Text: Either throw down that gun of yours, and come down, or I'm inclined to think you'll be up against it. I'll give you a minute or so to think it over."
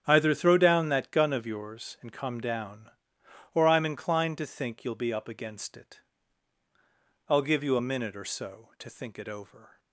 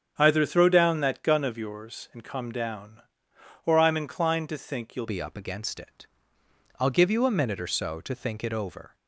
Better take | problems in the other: first | starts louder than the rest; strong; until 1.1 s; 8 dB; strong in the first // changes voice at "be"; from 5.0 s on; 3.9 s long

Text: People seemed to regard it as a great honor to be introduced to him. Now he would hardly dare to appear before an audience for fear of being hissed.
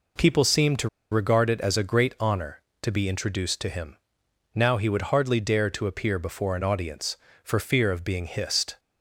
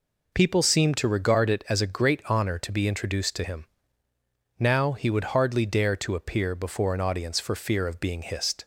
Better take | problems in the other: second | pauses between "to" and "regard"; slight; at 0.8 s; 0.22 s long

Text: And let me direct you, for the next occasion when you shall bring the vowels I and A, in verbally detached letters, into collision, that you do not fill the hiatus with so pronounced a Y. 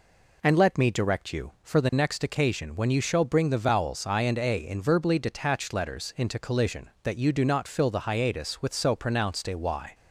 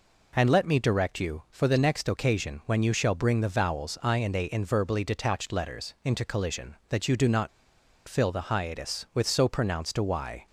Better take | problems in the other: first | pauses between "not" and "fill"; noticeable; at 7.4 s; 0.58 s long

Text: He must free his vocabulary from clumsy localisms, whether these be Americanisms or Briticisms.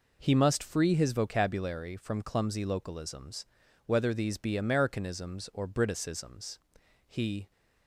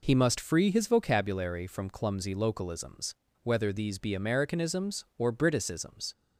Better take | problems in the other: second | goes on to say "He"; slight; from 7.0 s on; 0.42 s long

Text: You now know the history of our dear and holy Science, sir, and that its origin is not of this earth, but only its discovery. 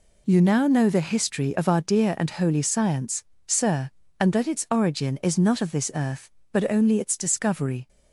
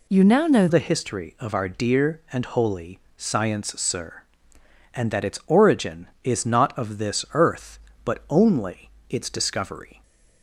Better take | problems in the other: first | changes voice at "the"; from 0.6 s on; 9.4 s long // pauses between "holy" and "Science"; slight; at 3.0 s; 0.18 s long // pauses between "only" and "its"; slight; at 8.9 s; 0.18 s long

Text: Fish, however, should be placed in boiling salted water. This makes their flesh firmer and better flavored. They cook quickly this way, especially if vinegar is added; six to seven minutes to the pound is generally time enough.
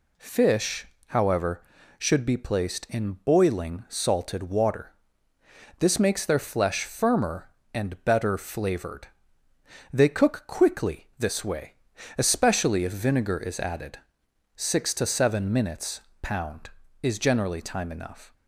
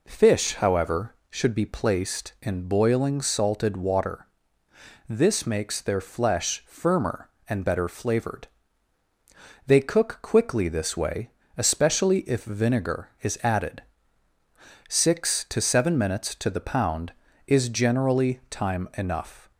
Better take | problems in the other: second | skips "to the"; at 16.1 s

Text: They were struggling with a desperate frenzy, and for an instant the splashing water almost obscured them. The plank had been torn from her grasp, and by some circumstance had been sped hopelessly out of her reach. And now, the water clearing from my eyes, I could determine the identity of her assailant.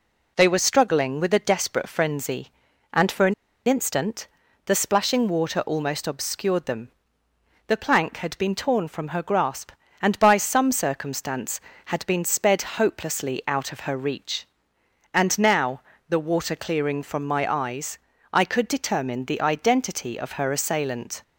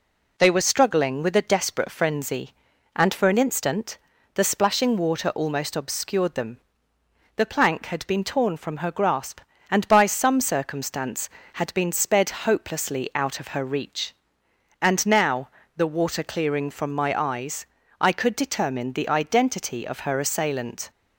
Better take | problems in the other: second | pauses between "an" and "instant"; slight; at 3.3 s; 0.32 s long // pauses between "instant" and "the"; at 4.2 s; 0.38 s long; also in the second

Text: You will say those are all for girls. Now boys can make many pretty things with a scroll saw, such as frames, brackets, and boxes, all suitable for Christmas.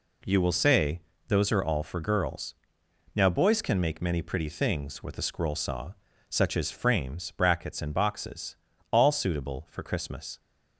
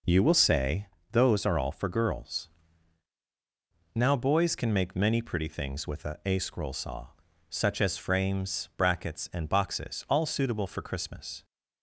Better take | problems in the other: first | pauses between "say" and "those"; slight; at 0.8 s; 0.28 s long; slight in the first // says "a" twice; at 6.2 s

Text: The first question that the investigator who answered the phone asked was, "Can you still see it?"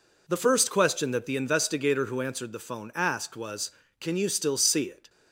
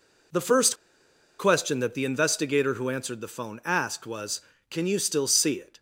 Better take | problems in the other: first | pauses between "first" and "question"; noticeable; at 0.7 s; 0.63 s long

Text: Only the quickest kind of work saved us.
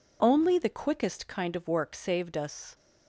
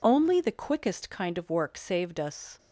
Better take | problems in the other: neither | none

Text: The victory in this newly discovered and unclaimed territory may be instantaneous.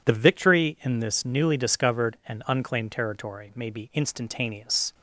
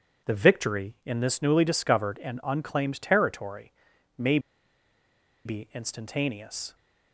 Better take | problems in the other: first | pauses between "territory" and "may"; at 3.7 s; 0.44 s long // pauses between "may" and "be"; at 4.3 s; 1.0 s long

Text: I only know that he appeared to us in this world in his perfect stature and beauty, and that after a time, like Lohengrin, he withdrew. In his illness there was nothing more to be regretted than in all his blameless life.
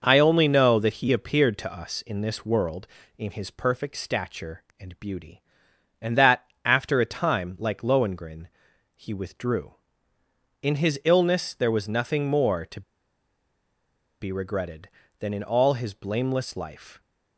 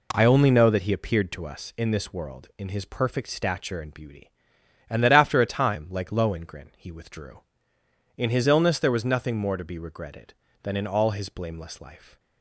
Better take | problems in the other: second | pauses between "that" and "after"; slight; at 6.4 s; 0.22 s long // pauses between "to" and "be"; strong; at 12.8 s; 1.3 s long

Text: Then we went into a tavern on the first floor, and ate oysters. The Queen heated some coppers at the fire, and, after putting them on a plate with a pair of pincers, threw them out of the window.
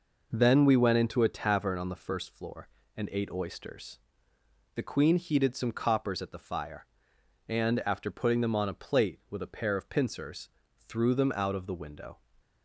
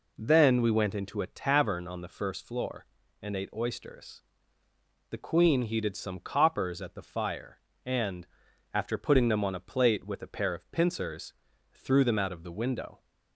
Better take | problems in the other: neither | none

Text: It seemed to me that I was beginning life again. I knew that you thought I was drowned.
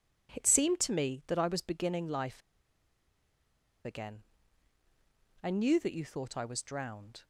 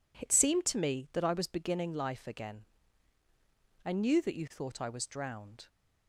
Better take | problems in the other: second | pauses between "life" and "again"; strong; at 2.4 s; 1.4 s long

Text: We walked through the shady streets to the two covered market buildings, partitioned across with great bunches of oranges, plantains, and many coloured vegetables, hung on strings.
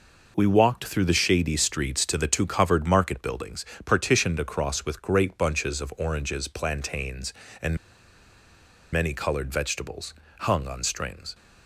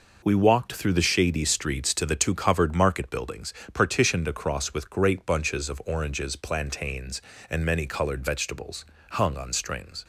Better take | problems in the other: second | pauses between "and" and "many"; at 7.7 s; 1.1 s long

